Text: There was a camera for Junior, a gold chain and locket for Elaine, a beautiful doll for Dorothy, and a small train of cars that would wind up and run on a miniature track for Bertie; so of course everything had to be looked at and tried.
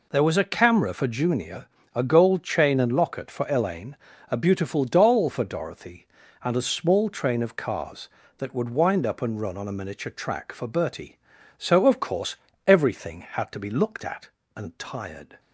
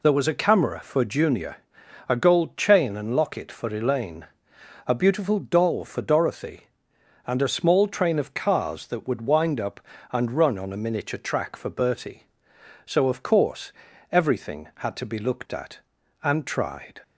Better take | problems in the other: second | pauses between "course" and "everything"; slight; at 12.3 s; 0.32 s long; also in the second // says "tired" for "tried"; at 14.7 s

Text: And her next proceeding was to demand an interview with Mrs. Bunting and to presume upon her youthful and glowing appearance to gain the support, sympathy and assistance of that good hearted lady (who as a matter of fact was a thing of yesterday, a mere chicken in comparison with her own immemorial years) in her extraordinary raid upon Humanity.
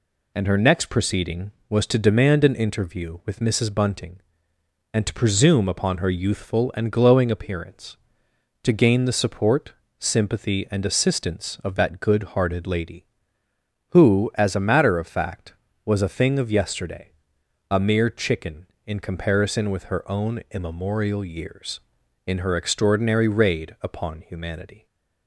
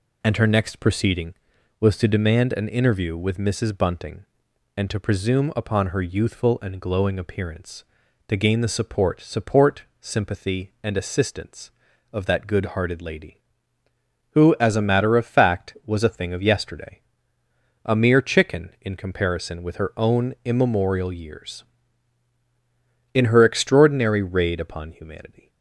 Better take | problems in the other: first | says "support" twice; at 9.2 s

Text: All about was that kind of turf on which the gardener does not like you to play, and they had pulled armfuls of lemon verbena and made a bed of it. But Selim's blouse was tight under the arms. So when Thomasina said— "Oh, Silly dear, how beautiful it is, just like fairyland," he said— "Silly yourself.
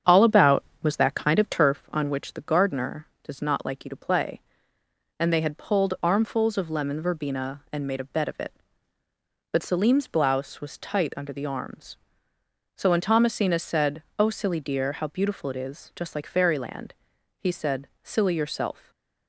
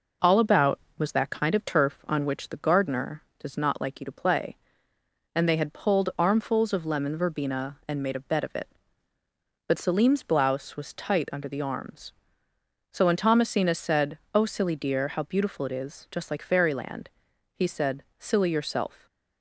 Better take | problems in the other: second | starts louder than the rest; strong; until 1.8 s; 8 dB

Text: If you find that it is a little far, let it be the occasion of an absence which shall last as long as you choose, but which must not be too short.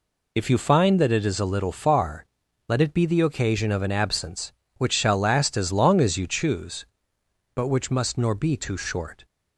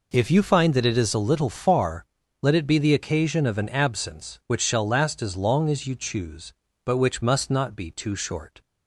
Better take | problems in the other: second | says "nor" for "not"; at 8.1 s

